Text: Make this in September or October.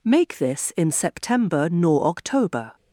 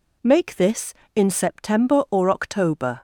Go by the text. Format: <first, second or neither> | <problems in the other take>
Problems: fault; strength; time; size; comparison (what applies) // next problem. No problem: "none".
second | says "nor" for "or"; at 1.6 s